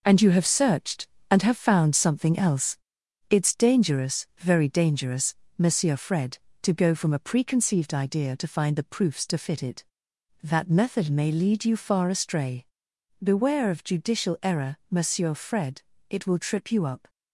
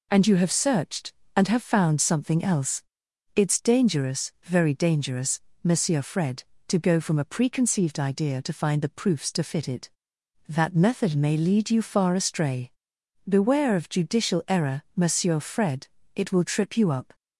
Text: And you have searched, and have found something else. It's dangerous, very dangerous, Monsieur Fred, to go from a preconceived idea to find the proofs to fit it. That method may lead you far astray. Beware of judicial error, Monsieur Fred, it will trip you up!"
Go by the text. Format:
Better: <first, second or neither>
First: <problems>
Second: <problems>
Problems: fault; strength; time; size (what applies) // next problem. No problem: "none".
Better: second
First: gets quieter; throughout; 7 dB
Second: none